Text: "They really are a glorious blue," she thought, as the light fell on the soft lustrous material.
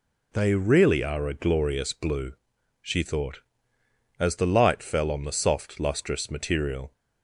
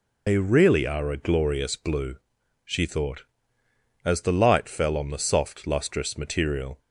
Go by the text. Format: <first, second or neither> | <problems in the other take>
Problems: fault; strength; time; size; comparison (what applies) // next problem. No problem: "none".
first | loses the start of "They"; at 0.2 s; 100 ms